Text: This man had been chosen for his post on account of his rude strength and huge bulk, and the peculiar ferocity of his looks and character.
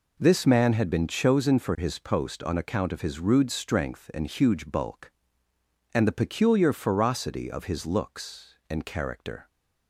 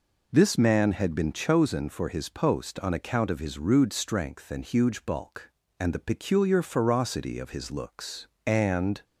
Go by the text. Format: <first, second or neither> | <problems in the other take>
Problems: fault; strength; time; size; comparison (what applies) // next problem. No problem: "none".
first | stops before "character"; at 9.0 s